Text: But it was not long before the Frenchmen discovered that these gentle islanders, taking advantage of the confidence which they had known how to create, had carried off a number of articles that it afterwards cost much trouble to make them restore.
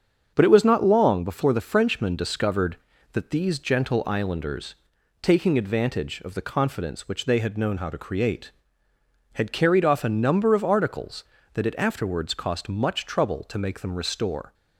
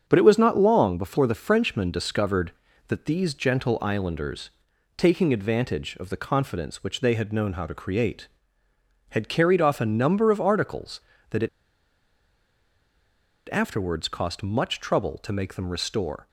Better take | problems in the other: first | starts louder than the rest; until 1.0 s; 7 dB; also in the first // pauses between "it" and "afterwards"; strong; at 11.4 s; 2.0 s long

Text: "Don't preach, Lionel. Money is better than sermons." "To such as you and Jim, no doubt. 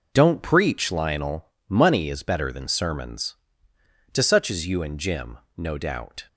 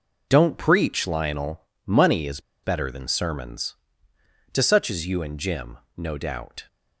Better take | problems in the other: first | pauses between "is" and "better"; slight; at 2.3 s; 0.23 s long

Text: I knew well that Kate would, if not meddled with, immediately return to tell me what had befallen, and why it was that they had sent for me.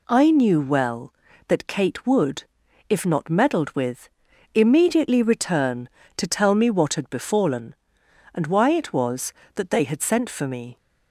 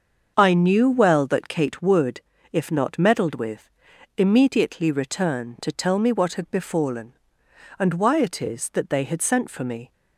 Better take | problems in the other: first | starts louder than the rest; until 1.3 s; 6.5 dB // says "is" for "was"; at 8.4 s

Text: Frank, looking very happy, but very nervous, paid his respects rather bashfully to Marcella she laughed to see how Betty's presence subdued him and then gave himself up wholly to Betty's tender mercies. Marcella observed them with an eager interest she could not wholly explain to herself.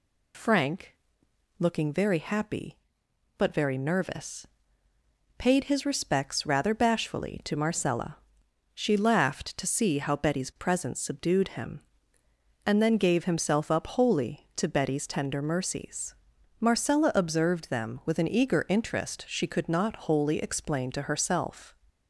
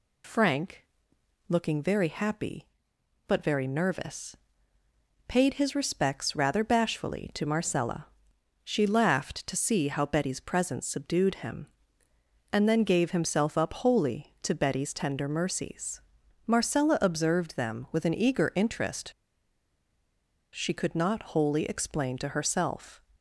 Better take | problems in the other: first | pauses between "Marcella" and "she"; noticeable; at 8.0 s; 0.60 s long; noticeable in the first // pauses between "interest" and "she"; strong; at 19.1 s; 1.4 s long

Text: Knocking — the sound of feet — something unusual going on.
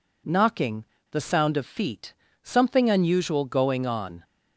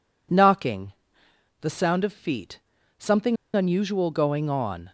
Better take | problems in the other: first | pauses between "something" and "unusual"; slight; at 3.3 s; 0.18 s long

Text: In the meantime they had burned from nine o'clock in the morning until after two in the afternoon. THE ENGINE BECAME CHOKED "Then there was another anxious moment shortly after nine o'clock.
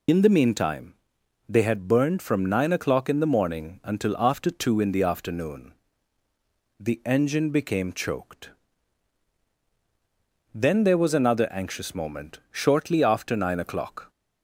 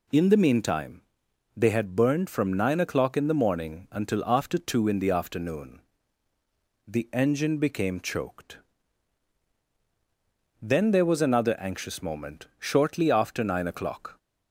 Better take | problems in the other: second | loses the start of "In"; at 0.0 s; 65 ms // pauses between "meantime" and "they"; noticeable; at 0.9 s; 0.52 s long; noticeable in the second // pauses between "CHOKED" and "Then"; strong; at 8.5 s; 2.0 s long; strong in the second

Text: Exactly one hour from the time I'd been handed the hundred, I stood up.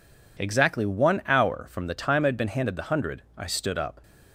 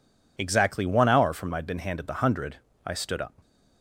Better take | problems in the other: first | skips "the time"; at 1.5 s

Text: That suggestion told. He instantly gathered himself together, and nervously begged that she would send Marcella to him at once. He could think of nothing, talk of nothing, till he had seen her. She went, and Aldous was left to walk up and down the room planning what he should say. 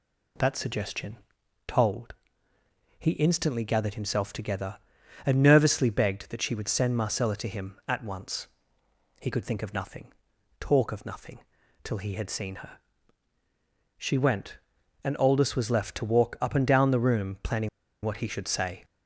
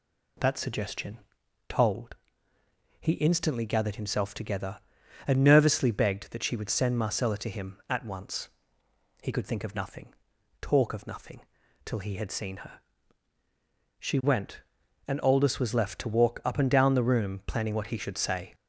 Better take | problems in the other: second | pauses between "suggestion" and "told"; noticeable; at 1.1 s; 0.50 s long; noticeable in the second // pauses between "planning" and "what"; slight; at 17.6 s; 0.35 s long

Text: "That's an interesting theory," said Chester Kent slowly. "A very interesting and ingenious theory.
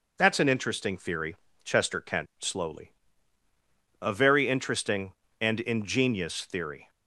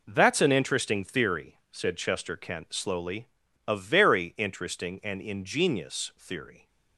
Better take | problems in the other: second | skips "said"; at 1.4 s

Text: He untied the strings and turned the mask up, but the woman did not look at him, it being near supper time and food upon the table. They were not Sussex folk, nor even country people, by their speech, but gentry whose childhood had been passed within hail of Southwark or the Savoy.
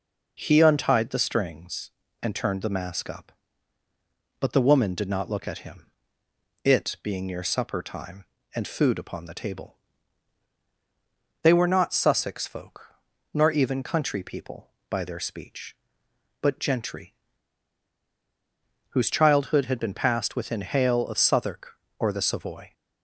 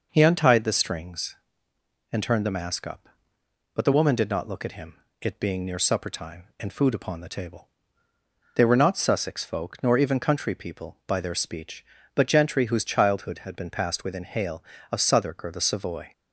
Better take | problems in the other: second | pauses between "gentry" and "whose"; strong; at 17.1 s; 1.7 s long

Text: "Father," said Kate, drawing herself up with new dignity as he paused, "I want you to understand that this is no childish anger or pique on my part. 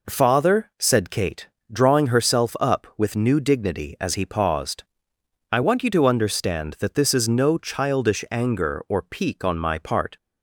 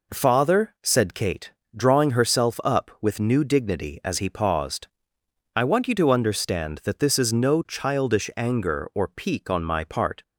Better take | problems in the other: neither | none

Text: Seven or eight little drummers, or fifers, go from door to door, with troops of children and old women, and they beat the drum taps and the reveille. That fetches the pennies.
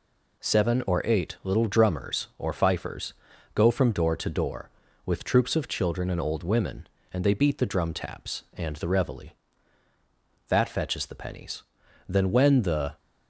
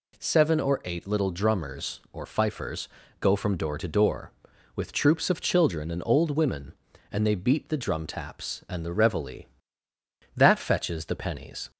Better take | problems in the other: second | goes on to say "Then when the"; noticeable; from 12.0 s on; 0.88 s long

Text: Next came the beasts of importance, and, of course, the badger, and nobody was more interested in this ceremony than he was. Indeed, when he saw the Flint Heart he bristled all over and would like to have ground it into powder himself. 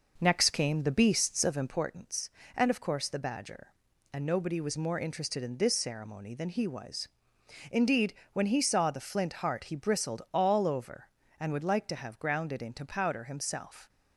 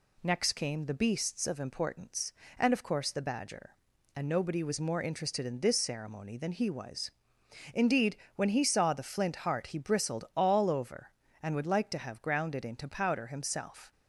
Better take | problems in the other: second | starts louder than the rest; noticeable; until 1.9 s; 5.5 dB

